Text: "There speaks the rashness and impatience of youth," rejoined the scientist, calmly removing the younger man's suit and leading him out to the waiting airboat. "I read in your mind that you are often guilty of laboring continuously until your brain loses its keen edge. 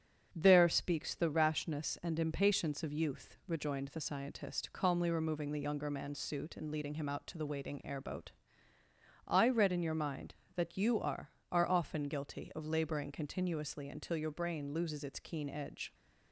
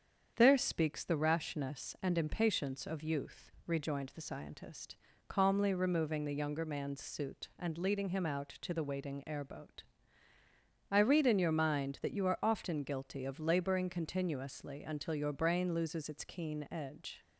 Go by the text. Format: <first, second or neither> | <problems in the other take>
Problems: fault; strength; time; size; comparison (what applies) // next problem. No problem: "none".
second | starts louder than the rest; strong; until 1.3 s; 7.5 dB; strong in the second // says "are" twice; at 11.5 s